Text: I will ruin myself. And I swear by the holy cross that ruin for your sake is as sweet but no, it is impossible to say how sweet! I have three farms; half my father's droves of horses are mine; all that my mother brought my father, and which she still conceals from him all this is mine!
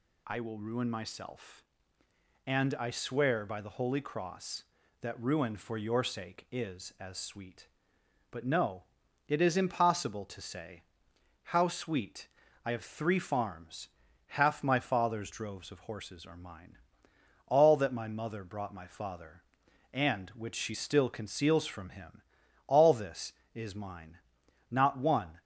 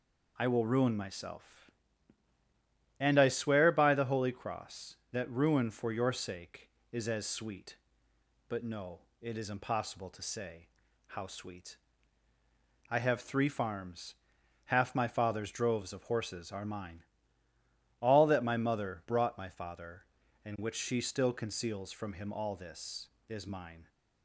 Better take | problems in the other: second | pauses between "say" and "how"; noticeable; at 10.8 s; 0.62 s long; also in the second // pauses between "him" and "all"; noticeable; at 22.2 s; 0.48 s long // goes on to say "Not one"; noticeable; from 24.7 s on; 0.70 s long

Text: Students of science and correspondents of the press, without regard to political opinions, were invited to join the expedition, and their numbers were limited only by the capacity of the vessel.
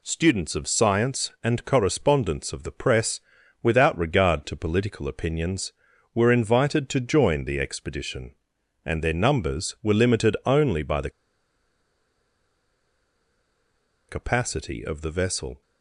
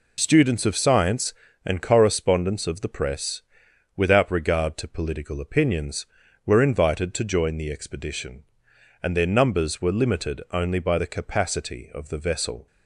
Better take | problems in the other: second | pauses between "the" and "capacity"; strong; at 11.1 s; 2.9 s long

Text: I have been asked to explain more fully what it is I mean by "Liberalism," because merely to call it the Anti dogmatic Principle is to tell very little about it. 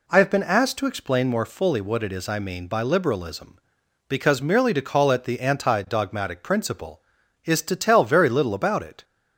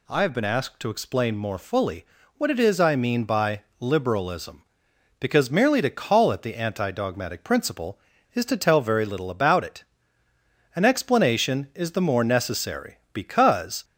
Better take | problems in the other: first | pauses between "fully" and "what"; slight; at 2.0 s; 0.32 s long // pauses between "by" and "Liberalism"; slight; at 3.6 s; 0.16 s long // goes on to say "An explanation is the more necessary because"; strong; from 10.7 s on; 3.1 s long

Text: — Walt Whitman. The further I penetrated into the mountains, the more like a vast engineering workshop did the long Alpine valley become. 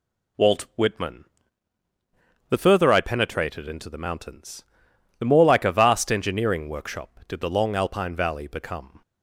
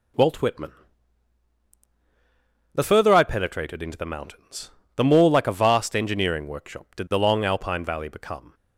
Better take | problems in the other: neither | none

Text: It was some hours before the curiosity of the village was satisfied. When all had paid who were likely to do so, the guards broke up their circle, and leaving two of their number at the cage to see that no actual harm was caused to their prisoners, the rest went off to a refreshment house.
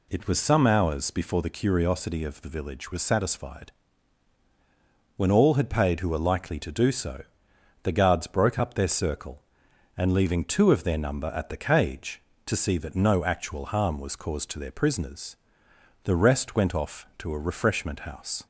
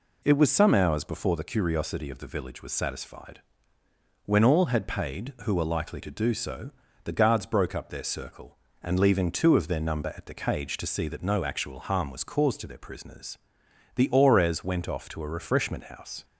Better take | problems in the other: first | says "aurez" for "rest"; at 14.1 s

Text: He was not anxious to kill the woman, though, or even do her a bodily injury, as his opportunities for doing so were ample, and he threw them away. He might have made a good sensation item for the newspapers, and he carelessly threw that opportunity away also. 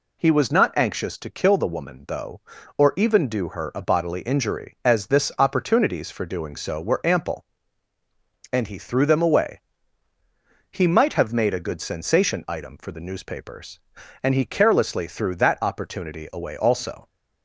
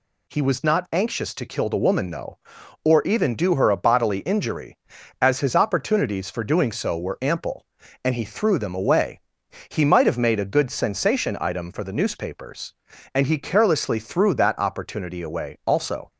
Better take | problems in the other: second | says "this" for "his"; at 5.0 s

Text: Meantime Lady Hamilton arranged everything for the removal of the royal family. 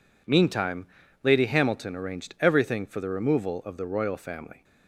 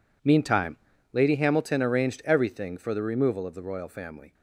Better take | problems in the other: neither | pauses between "Meantime" and "Lady"; the same in both

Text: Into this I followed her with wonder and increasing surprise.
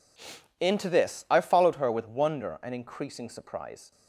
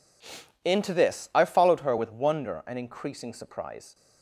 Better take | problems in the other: neither | none

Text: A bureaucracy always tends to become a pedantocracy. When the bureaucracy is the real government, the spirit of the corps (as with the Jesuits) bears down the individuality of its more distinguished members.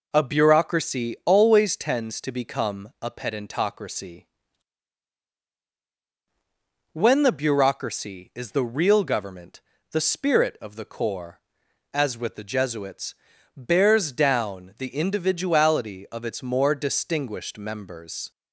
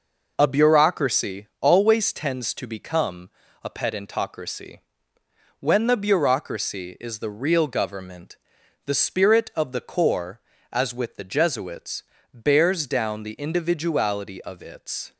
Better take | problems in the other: first | pauses between "become" and "a"; slight; at 3.2 s; 0.34 s long // stops before "more distinguished members"; at 15.1 s

